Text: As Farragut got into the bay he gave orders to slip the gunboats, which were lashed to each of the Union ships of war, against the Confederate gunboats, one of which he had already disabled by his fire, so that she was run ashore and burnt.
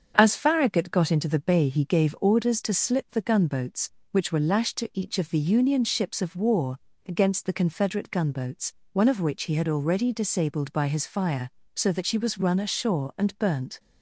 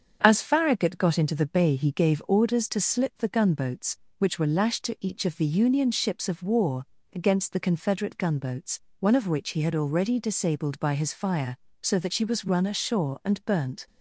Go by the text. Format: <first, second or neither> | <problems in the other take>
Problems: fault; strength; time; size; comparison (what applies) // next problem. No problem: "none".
neither | starts louder than the rest; strong; the same in both